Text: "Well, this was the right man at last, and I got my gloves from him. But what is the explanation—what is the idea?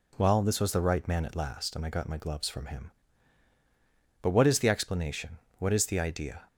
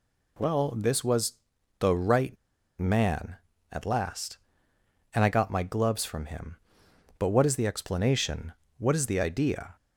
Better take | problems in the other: first | pauses between "was" and "the"; noticeable; at 1.3 s; 0.46 s long // pauses between "right" and "man"; at 2.3 s; 0.43 s long

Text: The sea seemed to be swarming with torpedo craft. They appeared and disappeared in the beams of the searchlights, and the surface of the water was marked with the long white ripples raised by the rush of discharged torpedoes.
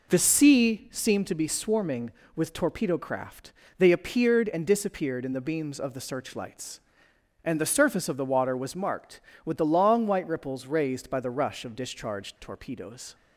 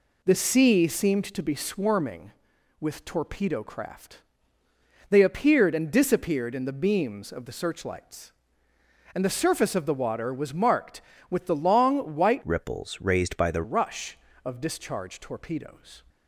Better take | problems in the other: first | changes voice from "ripples" to "the"; from 12.4 to 13.6 s; 1.2 s long

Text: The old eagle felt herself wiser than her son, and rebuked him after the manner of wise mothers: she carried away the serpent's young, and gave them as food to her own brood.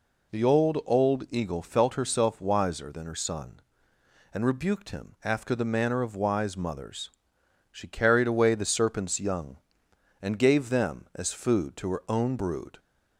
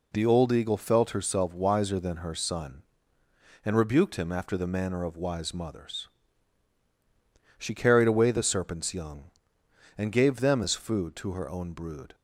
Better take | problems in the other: second | says "old" twice; at 0.8 s

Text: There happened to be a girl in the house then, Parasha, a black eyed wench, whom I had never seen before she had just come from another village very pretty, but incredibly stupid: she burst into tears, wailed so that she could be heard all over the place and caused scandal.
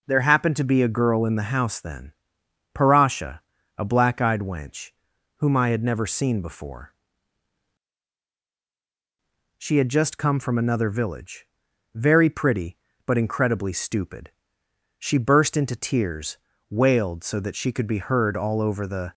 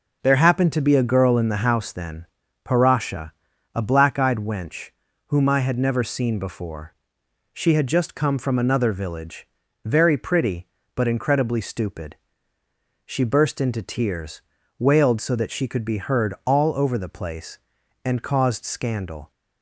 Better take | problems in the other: second | pauses between "before" and "she"; strong; at 6.8 s; 2.6 s long; noticeable in the second // pauses between "village" and "very"; noticeable; at 11.4 s; 0.50 s long; also in the second // stops before "place and caused scandal"; at 19.1 s

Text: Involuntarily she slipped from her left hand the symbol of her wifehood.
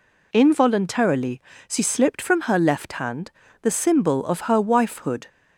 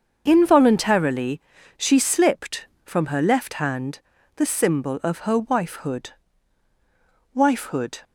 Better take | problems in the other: first | starts louder than the rest; until 1.2 s; 6.5 dB // pauses between "Involuntarily" and "she"; at 1.3 s; 0.38 s long; slight in the first // pauses between "hand" and "the"; at 3.9 s; 0.38 s long; slight in the first // says "wifehood" twice; at 7.3 s

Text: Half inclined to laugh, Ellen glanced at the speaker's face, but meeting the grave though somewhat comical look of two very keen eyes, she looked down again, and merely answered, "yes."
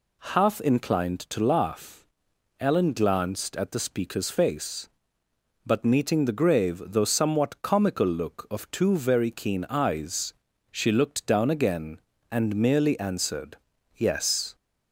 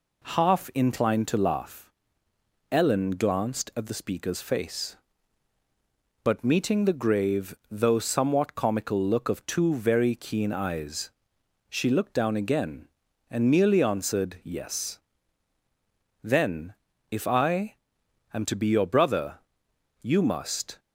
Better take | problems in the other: first | goes on to say "Then if I am to be your brother you must"; strong; from 16.2 s on; 4.5 s long

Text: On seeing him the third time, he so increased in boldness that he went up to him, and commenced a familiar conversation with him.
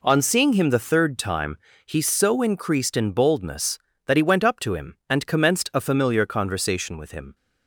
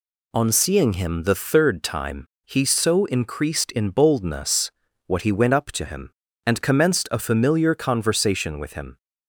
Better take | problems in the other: first | says "what" for "that"; at 5.0 s

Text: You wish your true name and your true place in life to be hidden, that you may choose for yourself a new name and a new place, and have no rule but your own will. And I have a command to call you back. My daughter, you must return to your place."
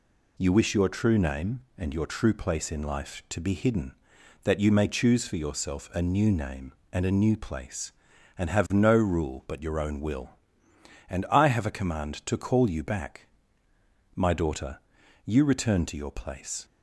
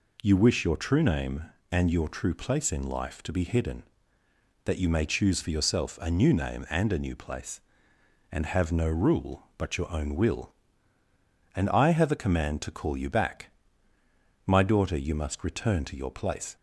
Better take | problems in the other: second | skips "must"; at 15.4 s

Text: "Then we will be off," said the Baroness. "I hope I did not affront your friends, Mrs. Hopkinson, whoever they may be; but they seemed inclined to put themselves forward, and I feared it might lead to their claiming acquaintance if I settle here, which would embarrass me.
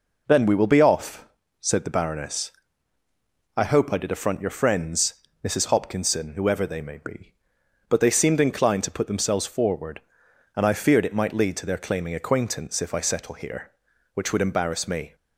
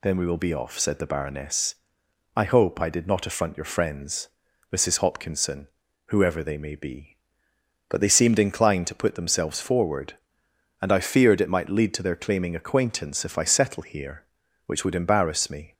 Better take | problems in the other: second | skips "not"; at 4.1 s

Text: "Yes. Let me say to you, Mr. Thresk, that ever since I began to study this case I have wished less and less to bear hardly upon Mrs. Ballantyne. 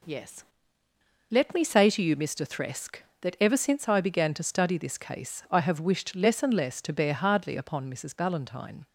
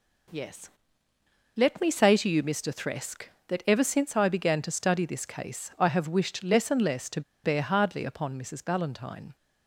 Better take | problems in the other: first | pauses between "to" and "bear"; slight; at 7.2 s; 0.23 s long

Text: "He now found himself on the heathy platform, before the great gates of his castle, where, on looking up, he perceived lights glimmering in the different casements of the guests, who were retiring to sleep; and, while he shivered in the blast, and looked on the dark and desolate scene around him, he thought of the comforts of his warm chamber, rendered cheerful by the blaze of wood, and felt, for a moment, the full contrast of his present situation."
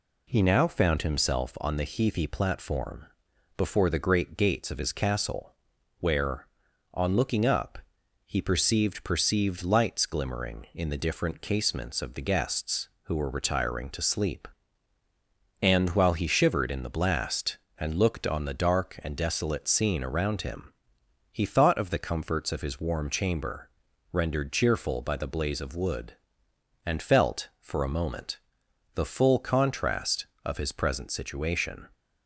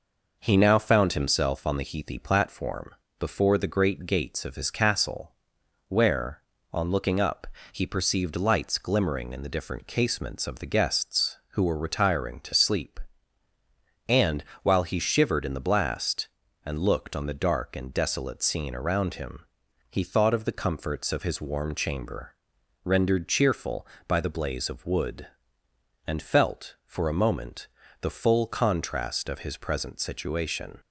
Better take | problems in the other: second | says "perceived" twice; at 9.0 s

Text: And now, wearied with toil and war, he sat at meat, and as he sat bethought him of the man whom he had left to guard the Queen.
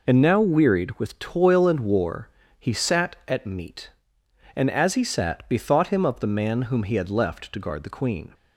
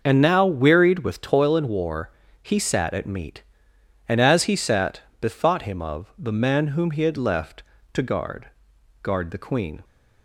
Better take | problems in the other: first | pauses between "sat" and "bethought"; slight; at 5.0 s; 0.18 s long // says "guard" twice; at 9.0 s

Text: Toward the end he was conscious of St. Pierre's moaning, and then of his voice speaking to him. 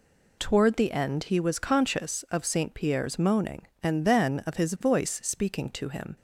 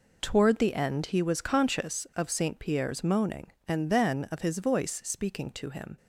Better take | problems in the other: first | gets quieter; strong; throughout; 10.5 dB

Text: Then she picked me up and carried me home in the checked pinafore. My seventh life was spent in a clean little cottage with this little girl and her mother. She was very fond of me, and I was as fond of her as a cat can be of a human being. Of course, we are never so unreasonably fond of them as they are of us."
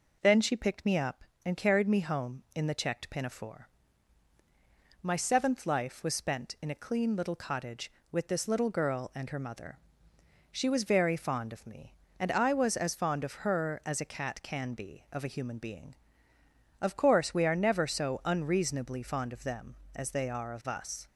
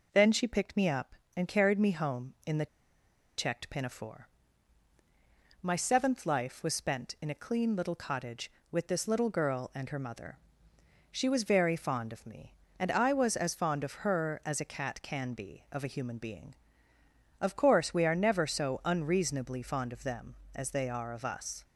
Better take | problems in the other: first | pauses between "the" and "checked"; noticeable; at 2.6 s; 0.71 s long

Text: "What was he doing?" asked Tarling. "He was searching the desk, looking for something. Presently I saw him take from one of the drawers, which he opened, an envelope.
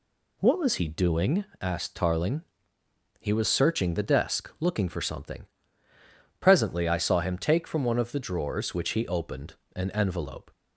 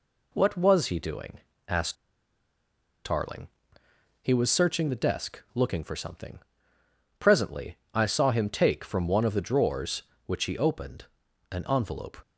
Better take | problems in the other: first | pauses between "asked" and "Tarling"; at 1.9 s; 1.0 s long // pauses between "Presently" and "I"; slight; at 7.7 s; 0.18 s long

